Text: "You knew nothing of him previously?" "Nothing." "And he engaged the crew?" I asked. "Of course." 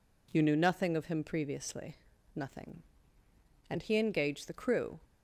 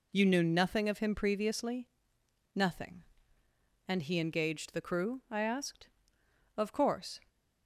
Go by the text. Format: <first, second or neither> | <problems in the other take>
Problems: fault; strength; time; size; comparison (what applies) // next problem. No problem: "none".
second | stops before "I asked Of course"; at 5.0 s